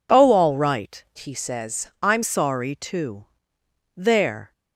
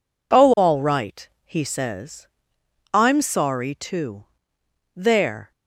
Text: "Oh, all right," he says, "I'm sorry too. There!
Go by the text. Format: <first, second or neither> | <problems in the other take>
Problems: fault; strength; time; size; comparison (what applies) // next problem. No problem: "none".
second | changes voice from "he" to "I'm"; from 1.1 to 2.2 s; 1.1 s long